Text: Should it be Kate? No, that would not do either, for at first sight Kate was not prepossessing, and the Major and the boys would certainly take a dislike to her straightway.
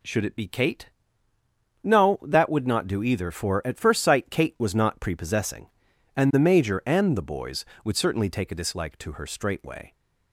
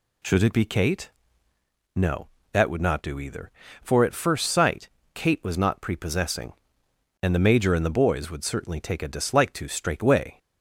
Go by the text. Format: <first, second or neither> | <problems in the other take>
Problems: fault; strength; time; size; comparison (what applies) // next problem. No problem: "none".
first | pauses between "sight" and "Kate"; slight; at 4.8 s; 0.26 s long // skips "her"; at 9.6 s